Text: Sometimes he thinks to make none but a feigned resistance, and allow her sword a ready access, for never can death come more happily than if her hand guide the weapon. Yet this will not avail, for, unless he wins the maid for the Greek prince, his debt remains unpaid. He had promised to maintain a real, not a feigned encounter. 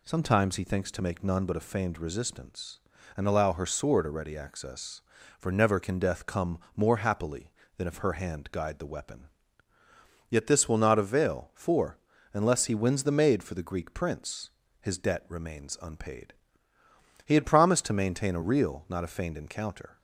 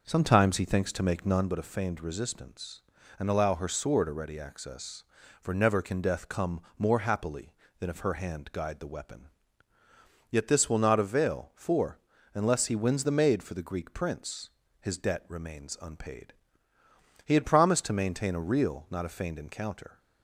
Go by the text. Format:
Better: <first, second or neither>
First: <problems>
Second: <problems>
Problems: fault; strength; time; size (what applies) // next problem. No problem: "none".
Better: first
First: pauses between "come" and "more"; slight; at 6.5 s; 0.16 s long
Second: starts louder than the rest; noticeable; until 1.5 s; 6 dB // pauses between "come" and "more"; slight; at 6.6 s; 0.16 s long